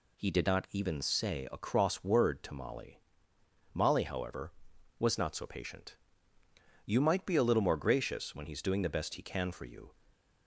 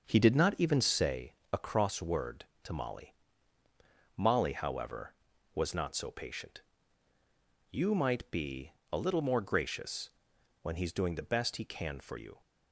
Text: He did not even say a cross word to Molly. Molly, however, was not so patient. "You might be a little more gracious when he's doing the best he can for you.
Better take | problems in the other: first | starts louder than the rest; until 1.2 s; 6.5 dB // pauses between "say" and "a"; slight; at 1.3 s; 0.18 s long // pauses between "be" and "a"; slight; at 8.7 s; 0.18 s long // pauses between "gracious" and "when"; noticeable; at 10.1 s; 0.52 s long

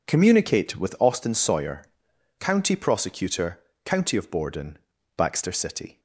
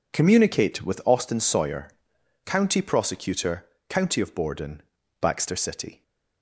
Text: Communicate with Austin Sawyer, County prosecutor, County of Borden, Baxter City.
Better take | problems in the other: neither | none

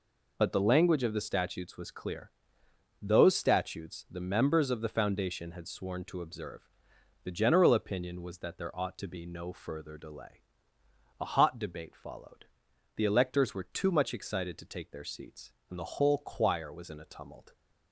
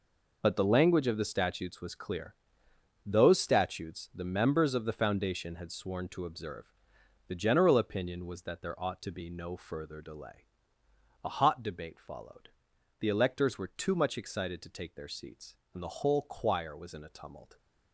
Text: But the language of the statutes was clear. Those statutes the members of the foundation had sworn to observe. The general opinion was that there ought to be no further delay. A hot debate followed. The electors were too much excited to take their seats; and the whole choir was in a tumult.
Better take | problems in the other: first | gets quieter; strong; throughout; 11 dB

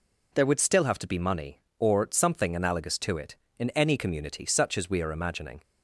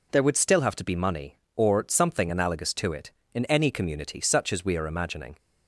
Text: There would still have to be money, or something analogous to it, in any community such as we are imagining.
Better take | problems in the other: neither | none

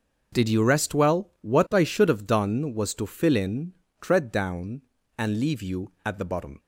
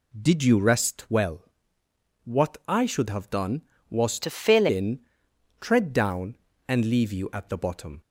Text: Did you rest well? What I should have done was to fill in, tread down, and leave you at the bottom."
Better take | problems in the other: first | changes voice from "to" to "fill"; from 4.2 to 4.6 s; 0.4 s long

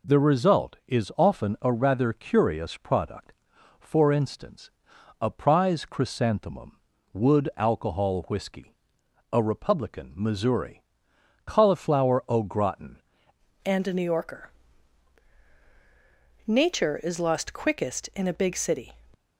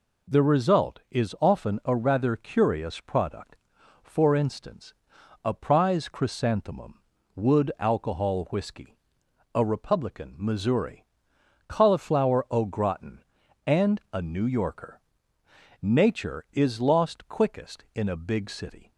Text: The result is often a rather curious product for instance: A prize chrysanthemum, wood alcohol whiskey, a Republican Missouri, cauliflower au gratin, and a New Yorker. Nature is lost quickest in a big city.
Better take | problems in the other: second | changes voice at "and"; from 13.6 s on; 5.3 s long

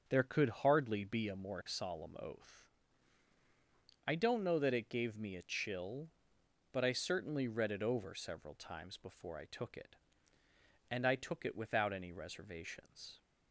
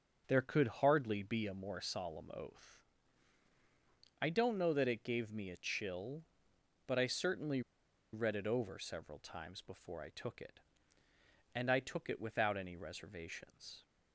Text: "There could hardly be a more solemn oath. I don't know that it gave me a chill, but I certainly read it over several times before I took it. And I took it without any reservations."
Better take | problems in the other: first | starts louder than the rest; until 1.2 s; 6 dB; also in the first // pauses between "certainly" and "read"; noticeable; at 7.6 s; 0.52 s long

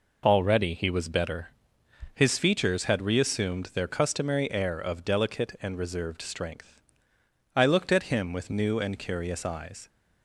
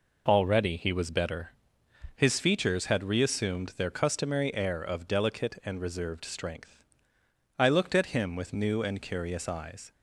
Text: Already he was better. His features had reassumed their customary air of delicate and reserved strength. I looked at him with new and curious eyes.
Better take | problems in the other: neither | none

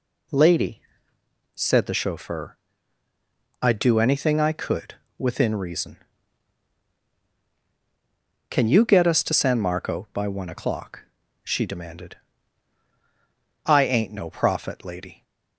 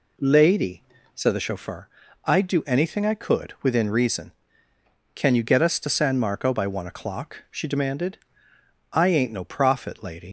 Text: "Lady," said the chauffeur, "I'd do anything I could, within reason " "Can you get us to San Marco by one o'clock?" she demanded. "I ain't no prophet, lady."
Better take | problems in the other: first | leaves "lady" unfinished; at 10.2 s; 105 ms

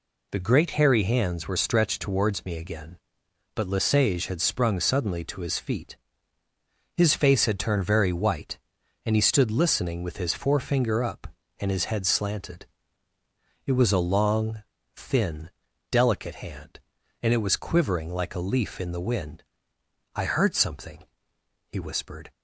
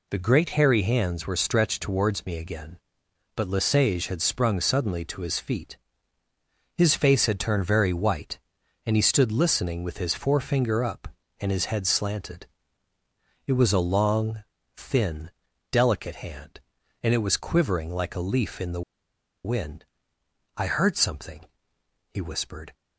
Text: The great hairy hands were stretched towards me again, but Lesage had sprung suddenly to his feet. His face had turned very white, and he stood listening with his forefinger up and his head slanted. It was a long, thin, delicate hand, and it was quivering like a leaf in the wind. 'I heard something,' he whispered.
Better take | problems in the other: first | pauses between "the" and "wind"; noticeable; at 18.8 s; 0.63 s long

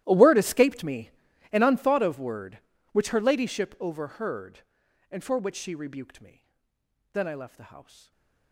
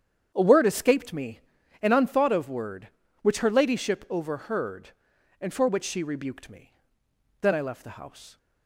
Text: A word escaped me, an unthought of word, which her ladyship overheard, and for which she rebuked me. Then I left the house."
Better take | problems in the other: second | gets quieter; strong; throughout; 22.5 dB // starts louder than the rest; strong; until 1.0 s; 14 dB; strong in the second // stays silent after the last word; slight; from 7.8 s on; 0.7 s long

